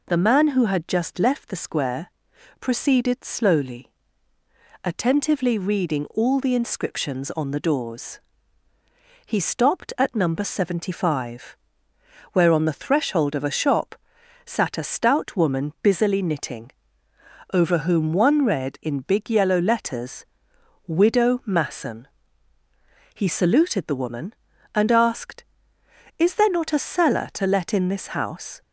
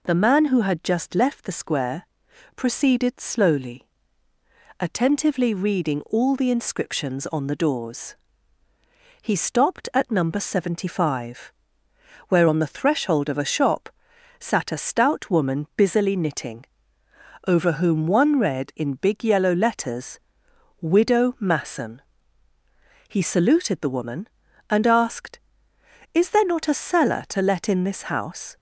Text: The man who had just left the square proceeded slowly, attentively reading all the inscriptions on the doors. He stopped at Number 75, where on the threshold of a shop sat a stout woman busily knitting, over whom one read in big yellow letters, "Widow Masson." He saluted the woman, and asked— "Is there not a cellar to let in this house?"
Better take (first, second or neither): neither